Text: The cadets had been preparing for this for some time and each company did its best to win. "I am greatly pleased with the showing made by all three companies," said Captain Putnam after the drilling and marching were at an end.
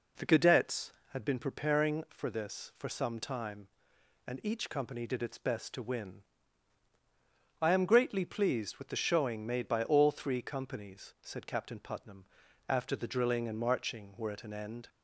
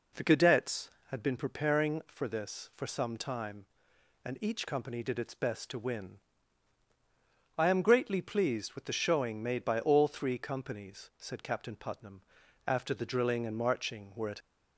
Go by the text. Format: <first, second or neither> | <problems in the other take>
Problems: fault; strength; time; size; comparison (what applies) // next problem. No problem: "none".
first | pauses between "Putnam" and "after"; noticeable; at 12.2 s; 0.46 s long; also in the first // stops before "an end"; at 14.4 s